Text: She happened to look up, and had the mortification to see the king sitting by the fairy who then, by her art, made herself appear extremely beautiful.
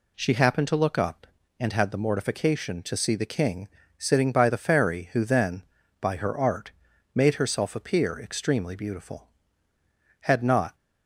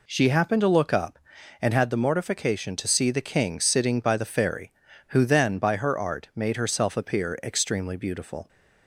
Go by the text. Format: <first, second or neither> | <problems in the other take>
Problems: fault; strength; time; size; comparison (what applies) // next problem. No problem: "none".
second | pauses between "king" and "sitting"; slight; at 3.6 s; 0.30 s long // goes on to say "Had not"; from 10.2 s on; 0.54 s long